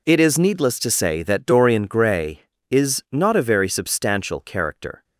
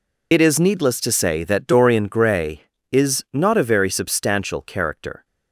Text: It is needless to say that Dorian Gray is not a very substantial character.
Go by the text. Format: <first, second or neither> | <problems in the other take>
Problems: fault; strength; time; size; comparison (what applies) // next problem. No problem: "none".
first | loses the start of "It"; at 0.3 s; 45 ms